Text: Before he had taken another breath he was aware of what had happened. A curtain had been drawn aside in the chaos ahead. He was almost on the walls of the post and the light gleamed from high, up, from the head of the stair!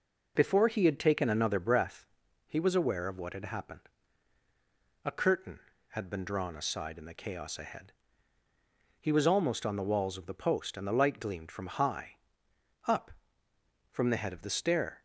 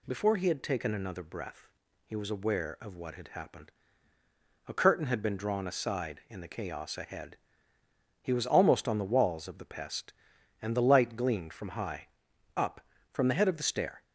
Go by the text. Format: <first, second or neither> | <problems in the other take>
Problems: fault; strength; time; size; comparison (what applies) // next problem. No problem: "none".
first | pauses between "breath" and "he"; at 1.6 s; 0.38 s long; also in the first // says "pest" for "post"; at 9.6 s